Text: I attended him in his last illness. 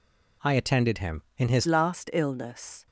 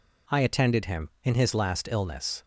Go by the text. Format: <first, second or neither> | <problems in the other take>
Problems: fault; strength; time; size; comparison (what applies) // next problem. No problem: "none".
second | changes voice at "last"; from 1.6 s on; 1.2 s long